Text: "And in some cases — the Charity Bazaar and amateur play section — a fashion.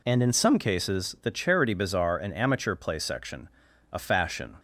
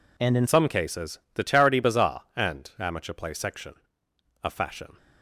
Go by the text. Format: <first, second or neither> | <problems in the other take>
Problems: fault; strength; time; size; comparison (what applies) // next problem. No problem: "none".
first | changes voice at "some"; from 0.4 s on; 4.5 s long